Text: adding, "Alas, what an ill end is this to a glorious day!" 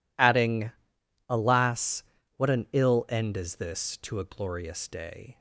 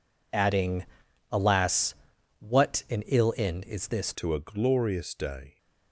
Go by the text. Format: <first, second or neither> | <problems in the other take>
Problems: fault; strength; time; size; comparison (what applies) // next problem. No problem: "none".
first | changes voice at "to"; from 4.1 s on; 1.4 s long